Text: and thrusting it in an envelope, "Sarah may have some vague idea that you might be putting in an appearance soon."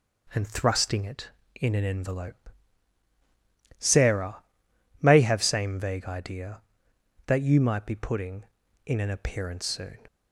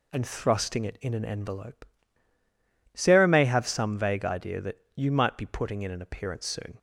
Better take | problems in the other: second | pauses between "Sarah" and "may"; noticeable; at 4.4 s; 0.58 s long // says "same" for "some"; at 5.4 s

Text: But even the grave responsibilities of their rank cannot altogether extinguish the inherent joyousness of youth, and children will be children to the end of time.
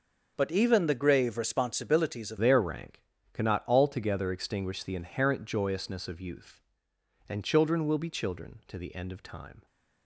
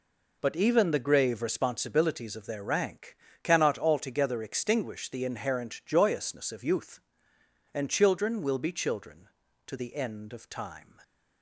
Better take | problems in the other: second | changes voice at "their"; from 2.3 s on; 7.3 s long // pauses between "rank" and "cannot"; slight; at 3.0 s; 0.30 s long; slight in the second

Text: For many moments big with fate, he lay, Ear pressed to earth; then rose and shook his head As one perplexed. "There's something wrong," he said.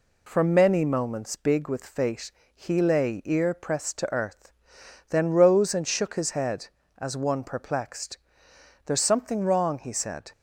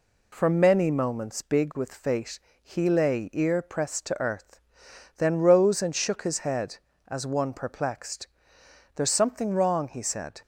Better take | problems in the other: neither | none

